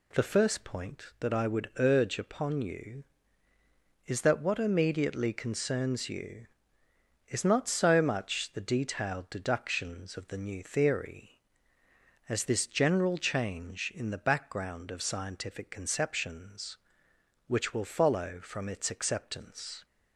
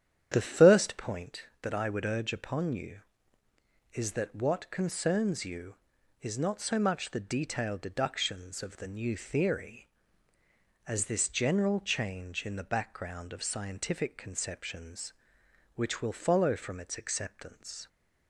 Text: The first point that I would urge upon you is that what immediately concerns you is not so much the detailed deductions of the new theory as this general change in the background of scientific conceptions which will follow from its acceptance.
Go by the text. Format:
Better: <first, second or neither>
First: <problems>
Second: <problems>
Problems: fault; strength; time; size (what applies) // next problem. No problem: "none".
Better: first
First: none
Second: starts louder than the rest; strong; until 1.3 s; 9.5 dB // skips "immediately"; at 4.7 s